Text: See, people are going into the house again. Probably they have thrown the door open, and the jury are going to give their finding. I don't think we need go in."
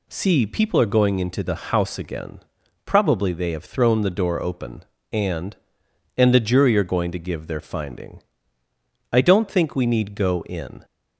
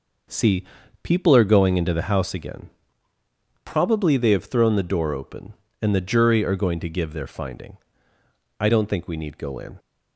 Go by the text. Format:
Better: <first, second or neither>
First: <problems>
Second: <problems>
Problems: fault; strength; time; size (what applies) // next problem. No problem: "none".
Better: second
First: says "and" twice; at 6.1 s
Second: none